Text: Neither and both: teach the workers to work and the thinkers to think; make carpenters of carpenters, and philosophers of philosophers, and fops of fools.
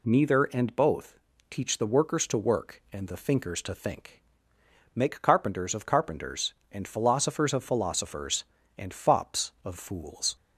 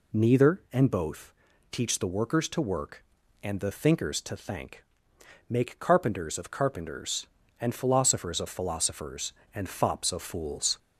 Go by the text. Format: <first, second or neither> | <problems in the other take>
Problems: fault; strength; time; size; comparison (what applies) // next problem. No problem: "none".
first | says "thank" for "think"; at 4.3 s